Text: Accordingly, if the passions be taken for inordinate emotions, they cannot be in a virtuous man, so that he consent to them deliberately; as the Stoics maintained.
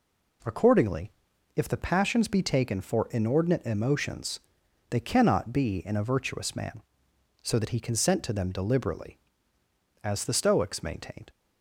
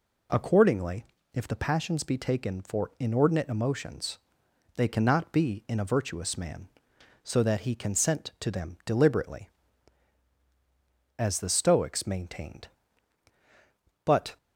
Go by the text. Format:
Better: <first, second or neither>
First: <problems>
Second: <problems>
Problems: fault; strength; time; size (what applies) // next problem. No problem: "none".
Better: first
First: none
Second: goes on to say "But"; slight; from 14.0 s on; 0.32 s long